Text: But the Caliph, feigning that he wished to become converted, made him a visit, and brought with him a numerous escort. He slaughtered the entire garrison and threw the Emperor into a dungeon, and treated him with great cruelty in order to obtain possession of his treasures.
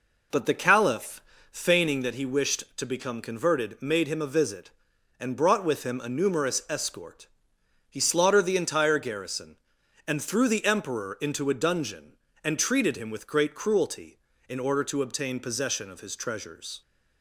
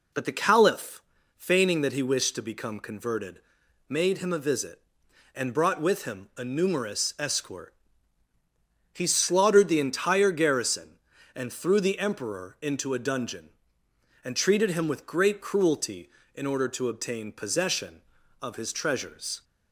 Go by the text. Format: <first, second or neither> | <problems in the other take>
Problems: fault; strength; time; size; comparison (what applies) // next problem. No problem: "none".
neither | none